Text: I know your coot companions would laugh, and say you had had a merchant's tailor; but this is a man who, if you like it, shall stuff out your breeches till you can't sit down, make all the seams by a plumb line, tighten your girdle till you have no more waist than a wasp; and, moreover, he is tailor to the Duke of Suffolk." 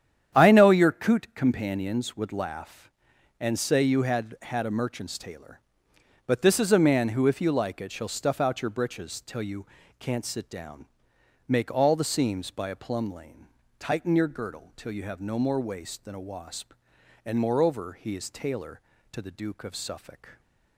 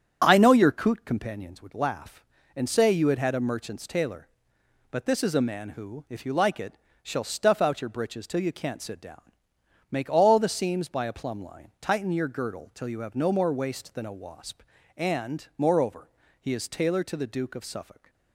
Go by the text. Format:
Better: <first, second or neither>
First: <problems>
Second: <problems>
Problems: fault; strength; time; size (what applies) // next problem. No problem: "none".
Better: second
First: starts louder than the rest; strong; until 1.4 s; 9.5 dB // pauses between "you" and "can't"; slight; at 9.6 s; 0.36 s long // says "lane" for "line"; at 13.1 s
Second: starts louder than the rest; strong; until 1.2 s; 8.5 dB